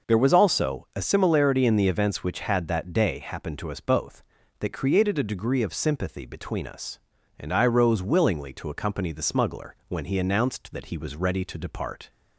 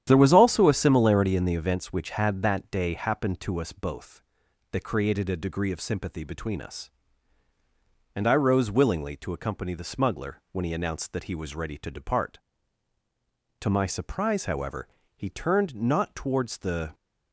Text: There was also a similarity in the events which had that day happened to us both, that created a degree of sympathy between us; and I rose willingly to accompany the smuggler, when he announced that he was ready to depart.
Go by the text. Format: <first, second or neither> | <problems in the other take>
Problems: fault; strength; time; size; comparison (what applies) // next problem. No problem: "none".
first | starts louder than the rest; strong; until 1.0 s; 10.5 dB // goes on to say "To my surprise however he turned not towards the"; strong; from 13.6 s on; 3.3 s long